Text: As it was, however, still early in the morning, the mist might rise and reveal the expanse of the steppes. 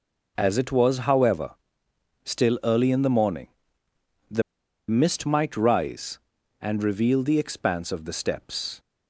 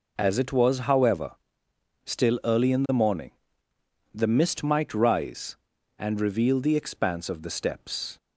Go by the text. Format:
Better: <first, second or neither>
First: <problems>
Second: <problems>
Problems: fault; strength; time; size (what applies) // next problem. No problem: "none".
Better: second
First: pauses between "the" and "mist"; noticeable; at 4.4 s; 0.47 s long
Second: none